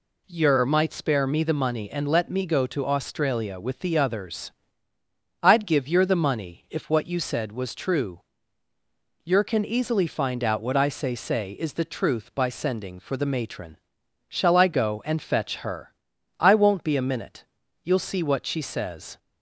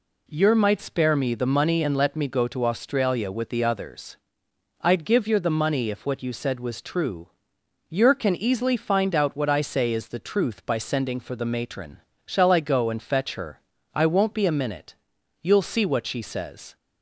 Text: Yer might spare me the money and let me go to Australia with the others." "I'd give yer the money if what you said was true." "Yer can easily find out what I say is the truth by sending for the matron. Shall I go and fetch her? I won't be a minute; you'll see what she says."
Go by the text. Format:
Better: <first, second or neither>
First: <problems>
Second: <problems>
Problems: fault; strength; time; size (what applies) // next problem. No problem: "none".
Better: second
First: says "say" twice; at 11.1 s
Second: none